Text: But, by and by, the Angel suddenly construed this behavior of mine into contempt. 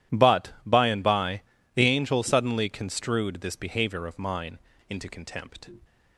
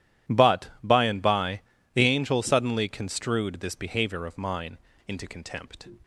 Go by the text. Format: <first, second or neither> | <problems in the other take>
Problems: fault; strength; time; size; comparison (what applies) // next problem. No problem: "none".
neither | pauses between "mine" and "into"; slight; the same in both